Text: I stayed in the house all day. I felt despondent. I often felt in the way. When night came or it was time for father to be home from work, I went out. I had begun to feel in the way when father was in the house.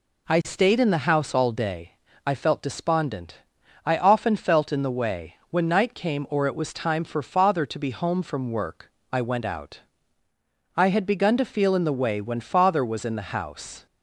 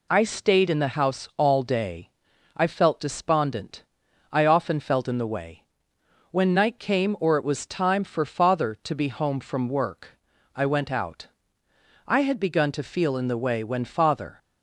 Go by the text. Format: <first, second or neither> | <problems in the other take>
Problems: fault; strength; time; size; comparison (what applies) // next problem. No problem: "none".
first | stops before "was in the house"; at 14.3 s